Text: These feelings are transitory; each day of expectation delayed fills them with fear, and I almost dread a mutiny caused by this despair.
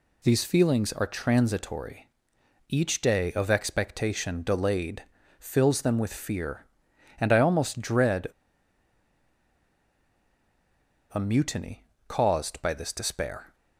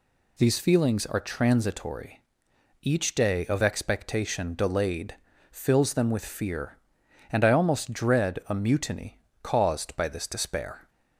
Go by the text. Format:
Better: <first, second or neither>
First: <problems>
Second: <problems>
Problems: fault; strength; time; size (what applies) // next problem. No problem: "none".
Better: second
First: pauses between "delayed" and "fills"; slight; at 5.0 s; 0.34 s long // pauses between "dread" and "a"; strong; at 8.2 s; 2.8 s long // pauses between "mutiny" and "caused"; slight; at 11.8 s; 0.22 s long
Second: pauses between "delayed" and "fills"; slight; at 5.1 s; 0.34 s long // pauses between "mutiny" and "caused"; slight; at 9.2 s; 0.22 s long